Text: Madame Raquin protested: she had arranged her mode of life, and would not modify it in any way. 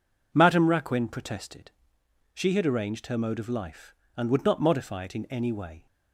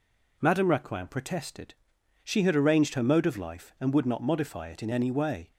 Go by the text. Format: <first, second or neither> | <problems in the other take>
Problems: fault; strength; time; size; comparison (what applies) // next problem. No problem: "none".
neither | none